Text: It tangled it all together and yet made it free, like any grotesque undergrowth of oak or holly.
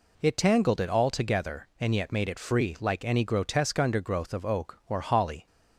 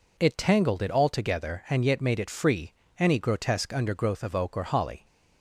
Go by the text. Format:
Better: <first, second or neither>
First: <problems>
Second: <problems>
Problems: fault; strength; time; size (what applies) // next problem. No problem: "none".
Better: first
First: none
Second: skips "like"; at 2.8 s